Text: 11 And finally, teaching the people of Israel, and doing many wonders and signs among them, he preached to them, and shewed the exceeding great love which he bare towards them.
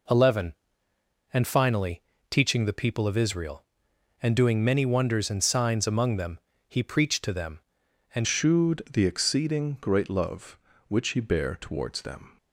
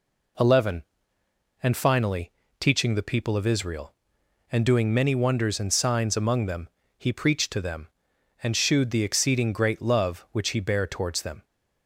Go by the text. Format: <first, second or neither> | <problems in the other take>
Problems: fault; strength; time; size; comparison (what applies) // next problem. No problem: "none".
second | changes voice at "shewed"; from 8.2 s on; 4.1 s long